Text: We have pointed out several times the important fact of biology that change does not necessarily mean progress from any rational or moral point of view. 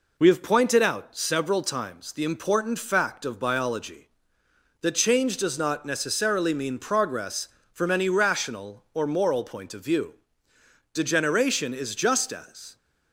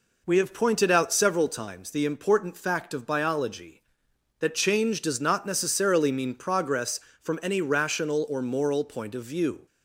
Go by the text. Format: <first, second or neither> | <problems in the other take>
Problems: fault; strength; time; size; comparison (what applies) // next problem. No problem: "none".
second | goes on to say "Degeneration is just as"; strong; from 10.9 s on; 1.8 s long